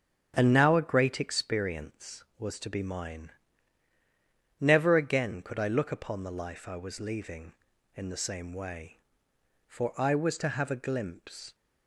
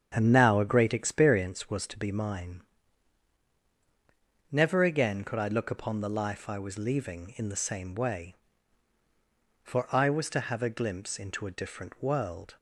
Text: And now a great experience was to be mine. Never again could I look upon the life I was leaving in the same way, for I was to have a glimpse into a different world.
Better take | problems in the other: second | starts louder than the rest; strong; until 1.3 s; 7.5 dB; strong in the second // stops before "into a different world"; at 11.5 s

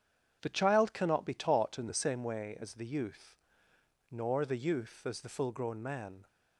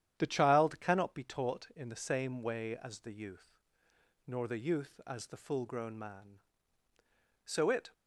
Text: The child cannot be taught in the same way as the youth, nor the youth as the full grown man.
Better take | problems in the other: first | starts louder than the rest; strong; until 1.2 s; 10 dB; strong in the first // goes on to say "So it"; slight; from 7.4 s on; 0.48 s long

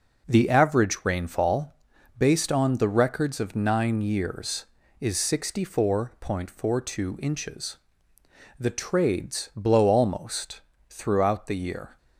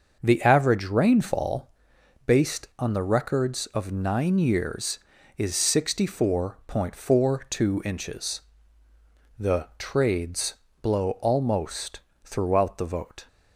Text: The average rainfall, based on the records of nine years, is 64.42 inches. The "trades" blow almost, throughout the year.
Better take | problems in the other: first | starts louder than the rest; until 1.2 s; 6 dB // pauses between "trades" and "blow"; slight; at 10.5 s; 0.26 s long // says "vote" for "year"; at 12.8 s

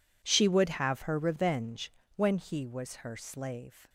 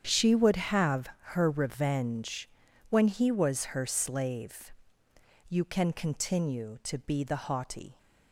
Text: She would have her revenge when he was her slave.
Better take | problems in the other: first | starts louder than the rest; strong; until 1.0 s; 8 dB // pauses between "have" and "her"; slight; at 1.0 s; 0.24 s long // pauses between "revenge" and "when"; at 2.4 s; 0.42 s long; slight in the first // goes on to say "You can continue to be the haughty"; strong; from 5.4 s on; 2.4 s long

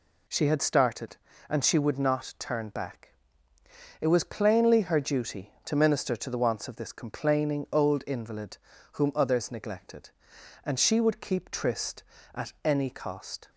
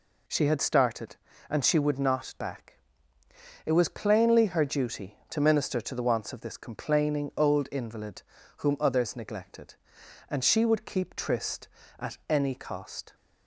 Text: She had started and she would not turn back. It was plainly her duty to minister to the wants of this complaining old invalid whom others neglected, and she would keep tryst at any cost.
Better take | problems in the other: first | skips "turn"; at 2.3 s // pauses between "invalid" and "whom"; slight; at 8.2 s; 0.36 s long; slight in the first

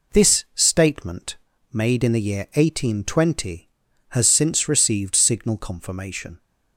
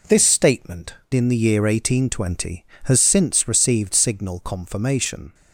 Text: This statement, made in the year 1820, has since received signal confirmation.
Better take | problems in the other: first | skips "made"; at 1.0 s

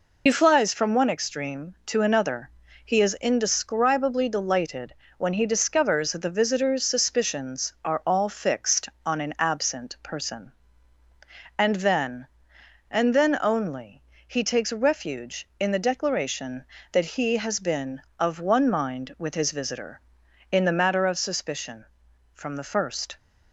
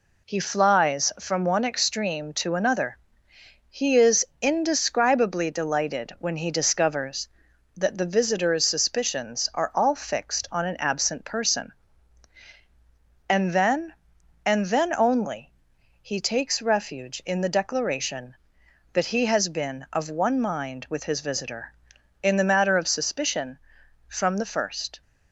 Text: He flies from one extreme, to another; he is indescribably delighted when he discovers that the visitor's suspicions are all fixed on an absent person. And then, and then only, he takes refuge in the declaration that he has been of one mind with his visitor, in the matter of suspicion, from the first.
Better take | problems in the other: second | loses the start of "He"; at 0.2 s; 55 ms // pauses between "delighted" and "when"; slight; at 4.9 s; 0.24 s long

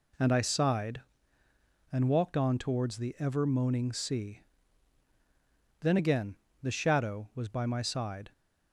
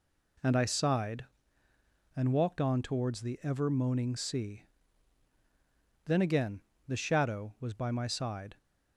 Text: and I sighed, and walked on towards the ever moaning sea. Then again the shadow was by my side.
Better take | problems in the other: neither | pauses between "again" and "the"; slight; the same in both

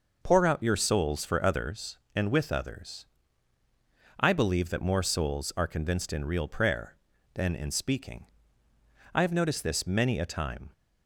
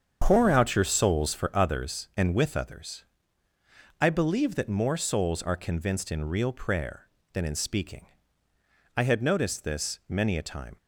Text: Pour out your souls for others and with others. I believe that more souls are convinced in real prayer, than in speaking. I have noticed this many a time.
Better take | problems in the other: first | starts louder than the rest; strong; until 1.2 s; 7.5 dB // says "had" for "have"; at 9.0 s

